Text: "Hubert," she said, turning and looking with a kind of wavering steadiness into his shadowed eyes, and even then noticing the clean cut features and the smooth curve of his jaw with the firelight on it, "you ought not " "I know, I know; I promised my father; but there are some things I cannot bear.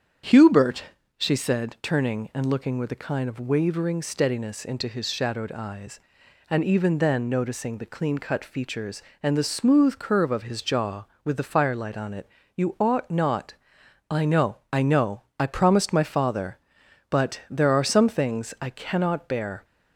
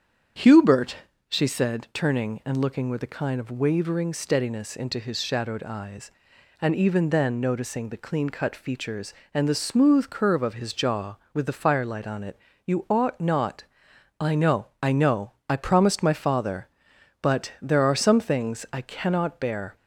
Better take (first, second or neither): neither